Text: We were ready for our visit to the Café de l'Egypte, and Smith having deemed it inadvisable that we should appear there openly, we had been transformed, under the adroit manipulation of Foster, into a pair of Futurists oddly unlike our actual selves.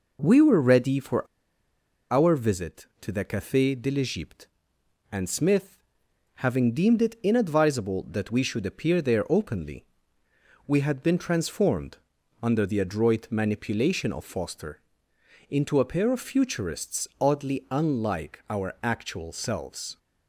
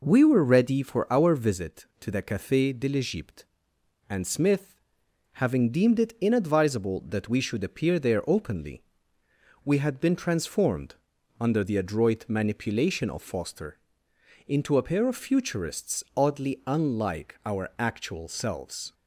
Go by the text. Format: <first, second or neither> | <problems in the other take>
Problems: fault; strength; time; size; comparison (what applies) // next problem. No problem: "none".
second | pauses between "for" and "our"; noticeable; at 1.2 s; 0.85 s long // pauses between "Smith" and "having"; noticeable; at 5.8 s; 0.54 s long; noticeable in the second